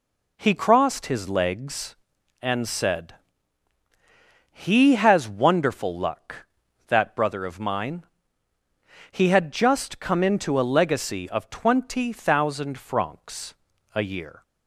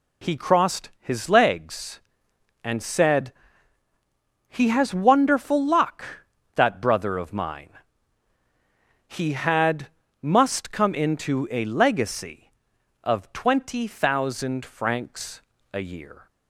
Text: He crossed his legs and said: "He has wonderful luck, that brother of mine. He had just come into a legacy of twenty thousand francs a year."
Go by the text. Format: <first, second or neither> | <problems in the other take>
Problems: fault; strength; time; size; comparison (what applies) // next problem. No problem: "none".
first | says "must" for "just"; at 10.2 s // pauses between "francs" and "a"; slight; at 15.4 s; 0.30 s long; also in the first